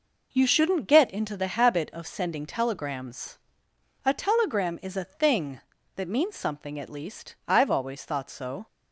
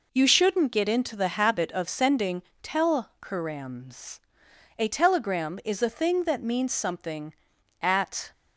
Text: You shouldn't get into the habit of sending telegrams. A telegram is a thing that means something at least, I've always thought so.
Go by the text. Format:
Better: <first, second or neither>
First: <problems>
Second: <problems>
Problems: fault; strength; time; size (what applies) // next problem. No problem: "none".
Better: first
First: none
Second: pauses between "sending" and "telegrams"; slight; at 2.4 s; 0.22 s long // stops before "least I've always thought so"; at 8.3 s